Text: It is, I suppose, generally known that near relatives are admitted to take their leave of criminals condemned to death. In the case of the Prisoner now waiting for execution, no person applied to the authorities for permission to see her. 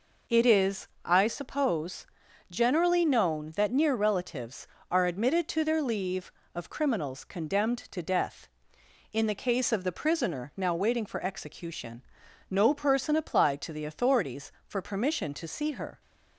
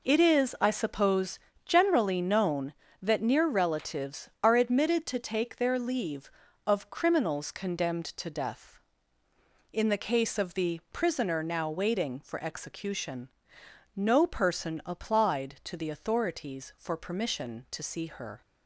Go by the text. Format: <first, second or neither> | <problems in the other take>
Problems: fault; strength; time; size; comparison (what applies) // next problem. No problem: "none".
second | skips "take"; at 5.6 s